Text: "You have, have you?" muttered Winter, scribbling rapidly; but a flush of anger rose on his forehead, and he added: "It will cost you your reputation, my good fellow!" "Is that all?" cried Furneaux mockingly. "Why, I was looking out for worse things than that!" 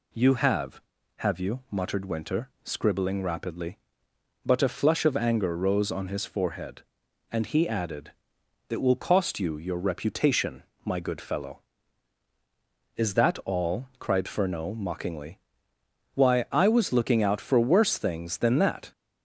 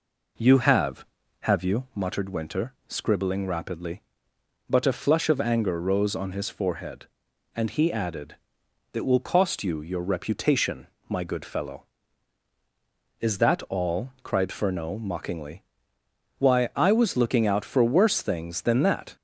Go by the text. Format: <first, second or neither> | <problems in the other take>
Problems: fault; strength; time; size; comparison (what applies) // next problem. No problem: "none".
first | starts louder than the rest; until 2.0 s; 4 dB